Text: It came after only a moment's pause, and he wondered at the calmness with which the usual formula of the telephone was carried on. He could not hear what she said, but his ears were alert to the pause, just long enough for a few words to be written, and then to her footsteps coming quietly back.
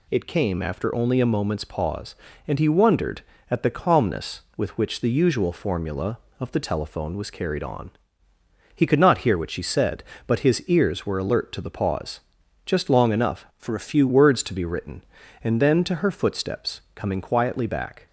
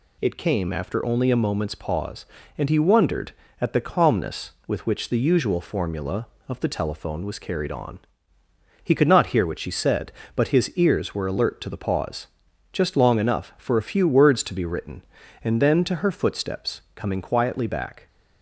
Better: second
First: changes voice from "for" to "few"; from 13.5 to 14.0 s; 0.5 s long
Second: none

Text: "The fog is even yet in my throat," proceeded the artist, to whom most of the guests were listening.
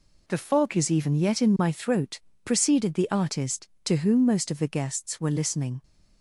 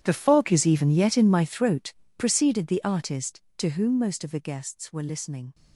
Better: first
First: none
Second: gets quieter; strong; throughout; 18 dB

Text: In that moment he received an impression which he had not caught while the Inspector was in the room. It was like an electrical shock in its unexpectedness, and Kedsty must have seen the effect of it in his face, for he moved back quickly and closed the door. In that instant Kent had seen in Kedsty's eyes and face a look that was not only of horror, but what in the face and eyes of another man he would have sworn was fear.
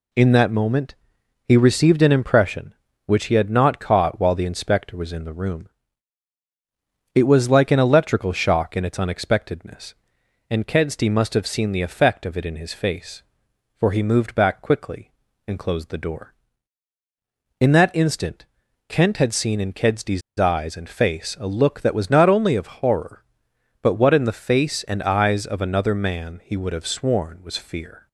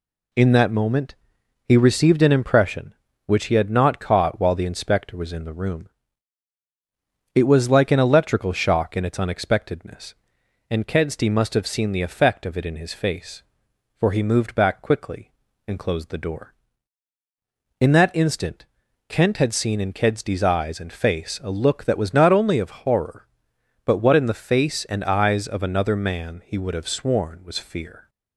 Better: second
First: pauses between "moment" and "he"; noticeable; at 0.9 s; 0.52 s long // pauses between "instant" and "Kent"; at 18.4 s; 0.44 s long // pauses between "Kedsty's" and "eyes"; slight; at 20.2 s; 0.18 s long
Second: pauses between "moment" and "he"; noticeable; at 1.1 s; 0.52 s long // pauses between "instant" and "Kent"; at 18.6 s; 0.44 s long

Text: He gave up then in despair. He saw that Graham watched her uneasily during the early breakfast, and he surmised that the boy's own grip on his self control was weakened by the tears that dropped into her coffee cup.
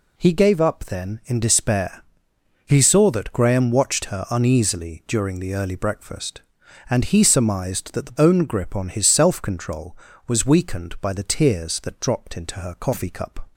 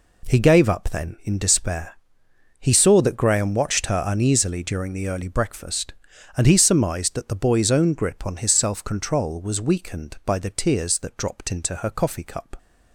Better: second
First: skips "boy's"; at 8.1 s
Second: none

